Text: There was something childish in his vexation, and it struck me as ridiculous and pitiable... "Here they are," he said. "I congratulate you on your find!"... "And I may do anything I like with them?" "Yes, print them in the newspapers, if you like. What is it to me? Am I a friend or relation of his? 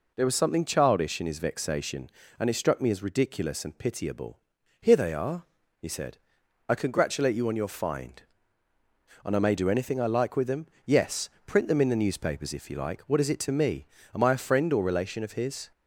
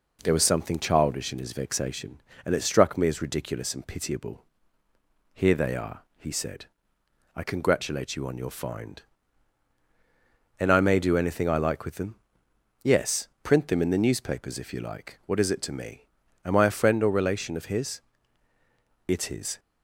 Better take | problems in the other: first | goes on to say "It is"; from 19.0 s on; 0.52 s long

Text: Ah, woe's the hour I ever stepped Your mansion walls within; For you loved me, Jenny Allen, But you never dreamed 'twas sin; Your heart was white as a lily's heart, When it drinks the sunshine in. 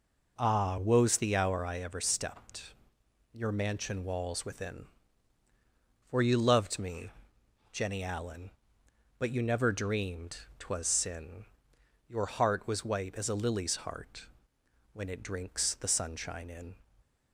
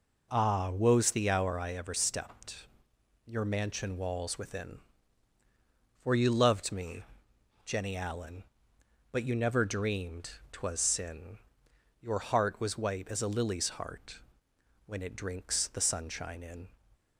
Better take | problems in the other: neither | pauses between "stepped" and "Your"; noticeable; the same in both // pauses between "dreamed" and "twas"; slight; the same in both

